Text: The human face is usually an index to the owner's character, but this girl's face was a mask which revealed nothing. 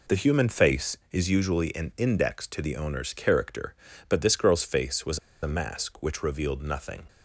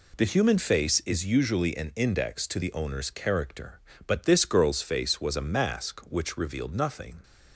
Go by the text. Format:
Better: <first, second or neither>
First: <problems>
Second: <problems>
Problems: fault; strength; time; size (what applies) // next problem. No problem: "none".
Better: second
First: pauses between "was" and "a"; slight; at 5.1 s; 0.25 s long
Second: none